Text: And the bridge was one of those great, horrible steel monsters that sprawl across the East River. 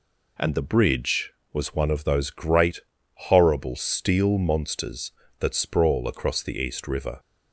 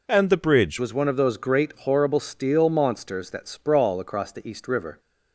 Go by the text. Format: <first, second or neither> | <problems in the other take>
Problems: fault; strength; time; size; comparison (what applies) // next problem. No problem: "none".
first | changes voice at "was"; from 0.7 s on; 4.2 s long